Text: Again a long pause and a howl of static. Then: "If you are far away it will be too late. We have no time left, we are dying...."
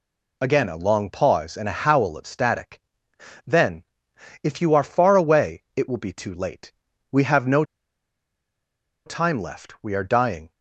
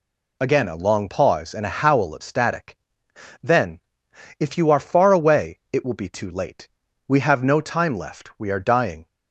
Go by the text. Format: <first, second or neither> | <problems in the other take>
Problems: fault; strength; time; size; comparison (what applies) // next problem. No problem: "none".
second | pauses between "no" and "time"; strong; at 7.6 s; 1.4 s long